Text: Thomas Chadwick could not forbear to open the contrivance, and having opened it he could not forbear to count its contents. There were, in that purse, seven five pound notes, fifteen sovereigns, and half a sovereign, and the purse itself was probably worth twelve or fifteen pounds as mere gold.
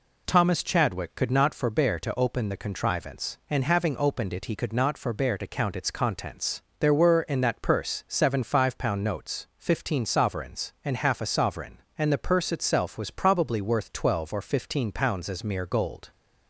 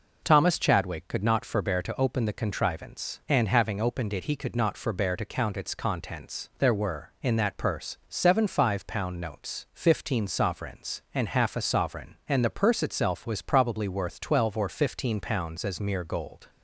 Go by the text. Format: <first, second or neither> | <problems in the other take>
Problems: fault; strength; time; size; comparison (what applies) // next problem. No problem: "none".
neither | none